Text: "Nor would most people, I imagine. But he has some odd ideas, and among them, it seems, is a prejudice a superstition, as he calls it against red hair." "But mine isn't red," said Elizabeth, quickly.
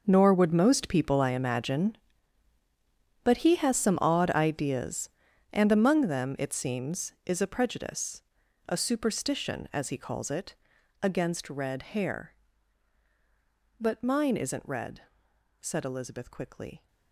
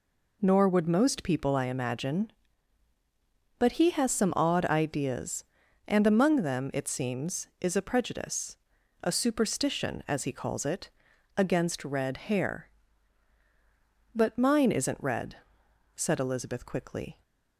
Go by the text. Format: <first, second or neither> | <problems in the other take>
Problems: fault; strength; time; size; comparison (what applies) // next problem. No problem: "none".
second | gets quieter; strong; throughout; 15.5 dB // pauses between "prejudice" and "a"; noticeable; at 8.2 s; 0.46 s long; noticeable in the second // pauses between "it" and "against"; noticeable; at 10.5 s; 0.48 s long; noticeable in the second